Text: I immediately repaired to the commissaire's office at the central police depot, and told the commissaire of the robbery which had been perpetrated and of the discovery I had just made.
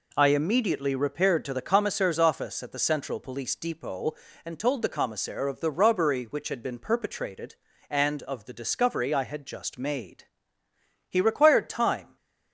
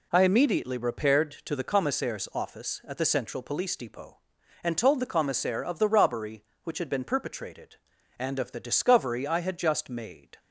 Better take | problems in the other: second | goes on to say "He required time"; noticeable; from 11.0 s on; 1.0 s long

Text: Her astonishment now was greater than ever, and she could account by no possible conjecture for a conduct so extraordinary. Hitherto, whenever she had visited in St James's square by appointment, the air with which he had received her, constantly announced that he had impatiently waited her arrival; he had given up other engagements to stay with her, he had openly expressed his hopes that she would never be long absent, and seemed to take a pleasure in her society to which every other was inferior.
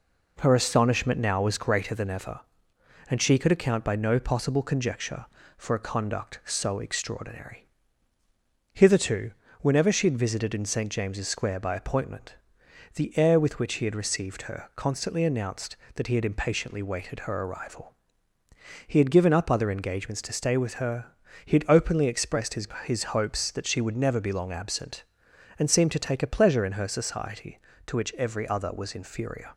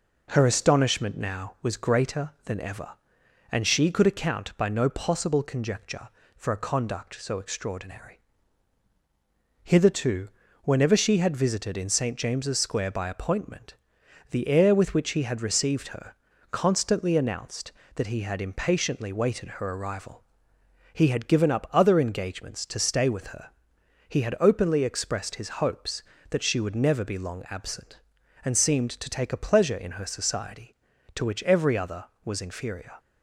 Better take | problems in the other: second | says "his" twice; at 22.8 s

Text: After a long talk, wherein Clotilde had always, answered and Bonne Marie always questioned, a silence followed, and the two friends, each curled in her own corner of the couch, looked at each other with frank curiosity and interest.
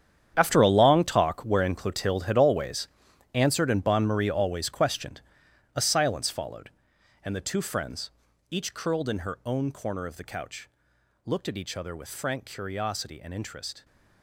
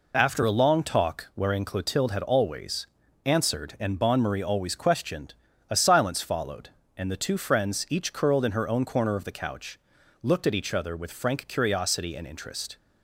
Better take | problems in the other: second | gets quieter; strong; throughout; 14 dB

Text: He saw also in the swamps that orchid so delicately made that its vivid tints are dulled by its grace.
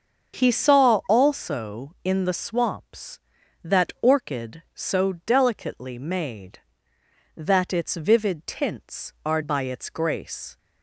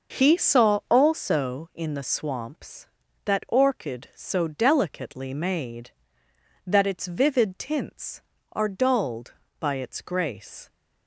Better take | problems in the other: second | starts louder than the rest; until 1.4 s; 6.5 dB; noticeable in the second // skips "dulled"; at 9.4 s

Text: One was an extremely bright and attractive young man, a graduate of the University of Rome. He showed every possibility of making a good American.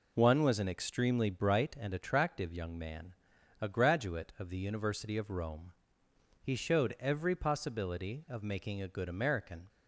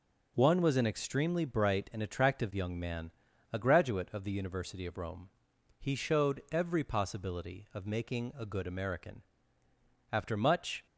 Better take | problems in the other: first | goes on to say "After much"; noticeable; from 10.1 s on; 0.74 s long

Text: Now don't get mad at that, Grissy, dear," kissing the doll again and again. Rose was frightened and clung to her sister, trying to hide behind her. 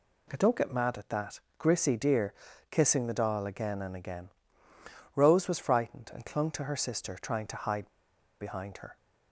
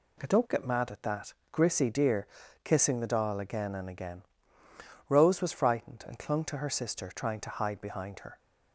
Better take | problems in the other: second | pauses between "hide" and "behind"; noticeable; at 7.8 s; 0.53 s long

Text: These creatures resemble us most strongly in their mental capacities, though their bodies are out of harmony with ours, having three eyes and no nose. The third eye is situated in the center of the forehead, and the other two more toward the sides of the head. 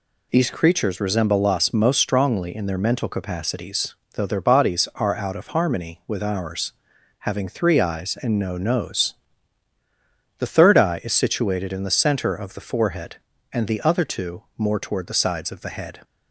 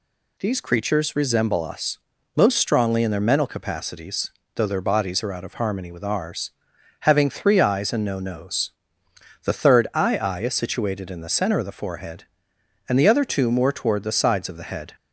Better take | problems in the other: first | pauses between "us" and "most"; at 1.9 s; 0.38 s long // says "eye" twice; at 10.1 s

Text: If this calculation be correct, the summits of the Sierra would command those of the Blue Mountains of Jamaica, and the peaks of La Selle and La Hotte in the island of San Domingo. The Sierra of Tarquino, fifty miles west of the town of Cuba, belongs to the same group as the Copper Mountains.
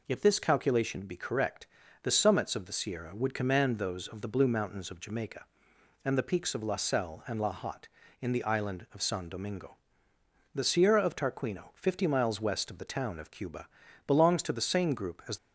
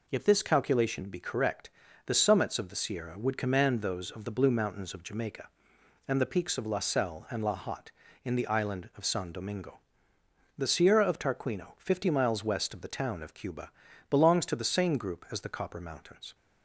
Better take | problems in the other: second | stops before "the Copper Mountains"; at 15.3 s

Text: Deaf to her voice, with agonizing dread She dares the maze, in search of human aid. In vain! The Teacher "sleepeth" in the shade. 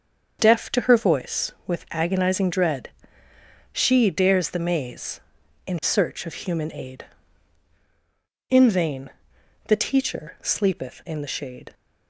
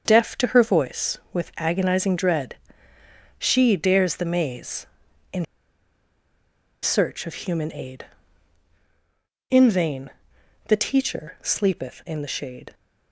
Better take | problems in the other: first | starts louder than the rest; until 1.0 s; 7 dB; also in the first // pauses between "dread" and "She"; noticeable; at 2.5 s; 0.86 s long; noticeable in the first // pauses between "in" and "search"; strong; at 5.4 s; 1.3 s long

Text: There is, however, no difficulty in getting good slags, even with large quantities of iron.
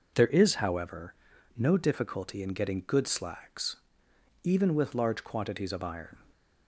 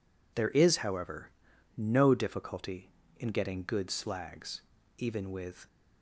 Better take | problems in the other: first | stops before "large quantities of iron"; at 5.6 s

